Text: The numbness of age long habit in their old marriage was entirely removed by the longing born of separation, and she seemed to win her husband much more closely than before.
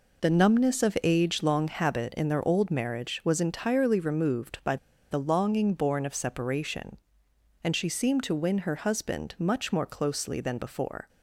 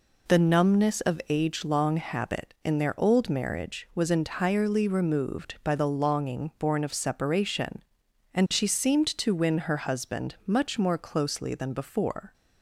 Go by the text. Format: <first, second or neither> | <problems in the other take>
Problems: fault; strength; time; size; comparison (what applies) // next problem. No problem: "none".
second | pauses between "by" and "the"; slight; at 4.7 s; 0.35 s long